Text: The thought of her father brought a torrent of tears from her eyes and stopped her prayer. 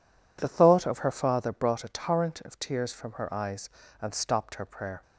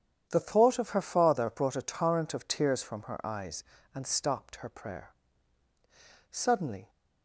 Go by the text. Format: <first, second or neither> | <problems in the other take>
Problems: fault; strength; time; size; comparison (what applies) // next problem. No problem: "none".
first | starts louder than the rest; strong; until 1.3 s; 9 dB // goes on to say "Suddenly"; from 6.3 s on; 0.58 s long